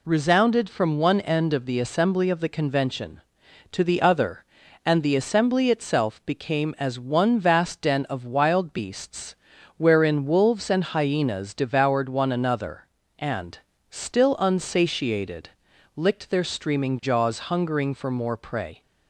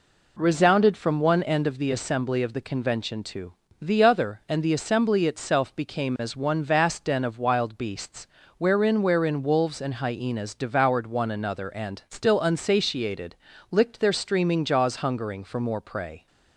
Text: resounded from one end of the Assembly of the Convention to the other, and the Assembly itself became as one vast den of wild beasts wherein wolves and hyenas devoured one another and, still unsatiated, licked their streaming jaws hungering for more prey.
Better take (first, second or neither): first